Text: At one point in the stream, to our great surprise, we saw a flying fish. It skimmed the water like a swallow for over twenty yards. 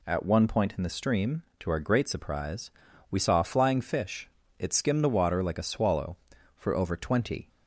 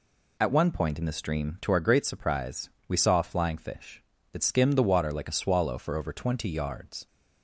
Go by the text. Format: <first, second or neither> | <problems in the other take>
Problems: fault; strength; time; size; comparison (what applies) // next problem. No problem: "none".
second | stops before "yards"; at 7.4 s